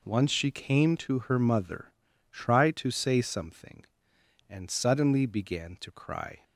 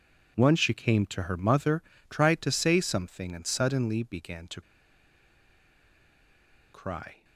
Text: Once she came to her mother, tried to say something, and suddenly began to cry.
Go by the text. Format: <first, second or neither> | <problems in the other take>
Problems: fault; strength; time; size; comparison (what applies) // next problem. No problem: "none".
first | pauses between "to" and "cry"; strong; at 4.6 s; 2.1 s long